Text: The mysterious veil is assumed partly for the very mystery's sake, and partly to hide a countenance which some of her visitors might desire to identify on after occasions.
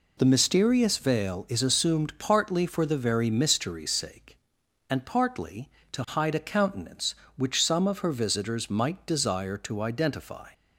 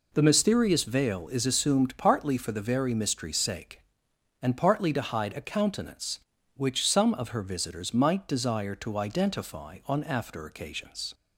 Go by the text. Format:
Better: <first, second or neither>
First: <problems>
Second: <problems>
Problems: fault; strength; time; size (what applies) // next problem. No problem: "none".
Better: second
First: stops before "on after occasions"; at 10.5 s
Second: none